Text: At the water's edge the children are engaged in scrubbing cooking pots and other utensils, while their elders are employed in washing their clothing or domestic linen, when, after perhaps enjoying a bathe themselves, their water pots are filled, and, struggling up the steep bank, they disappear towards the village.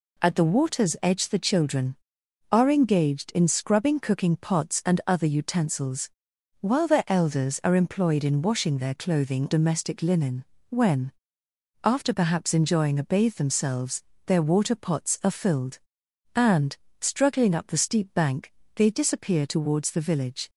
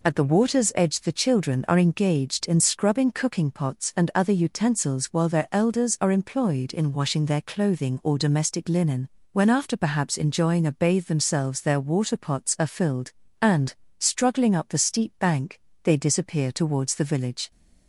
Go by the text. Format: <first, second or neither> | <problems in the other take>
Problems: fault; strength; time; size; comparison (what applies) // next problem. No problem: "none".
second | skips "or"; at 9.4 s